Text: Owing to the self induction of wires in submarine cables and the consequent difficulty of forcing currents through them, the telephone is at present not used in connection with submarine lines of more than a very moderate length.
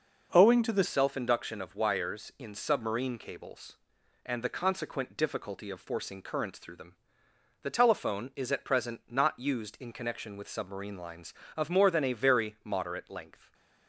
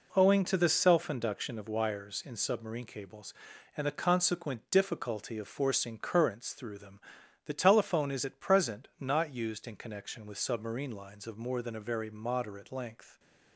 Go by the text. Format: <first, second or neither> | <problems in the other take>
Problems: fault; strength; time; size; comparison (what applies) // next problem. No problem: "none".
second | changes voice at "self"; from 0.8 s on; 12.7 s long // stays silent after the last word; slight; from 13.3 s on; 0.5 s long